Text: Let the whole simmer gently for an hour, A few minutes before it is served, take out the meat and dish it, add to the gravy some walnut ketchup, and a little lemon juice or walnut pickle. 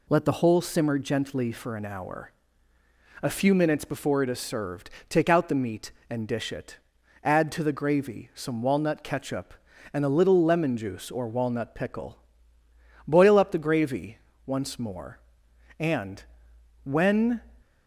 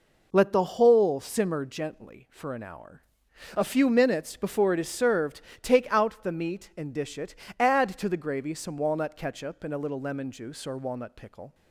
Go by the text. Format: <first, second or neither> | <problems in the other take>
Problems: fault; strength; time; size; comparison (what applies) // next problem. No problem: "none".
second | goes on to say "Boil up the gravy once more and when"; strong; from 13.0 s on; 4.3 s long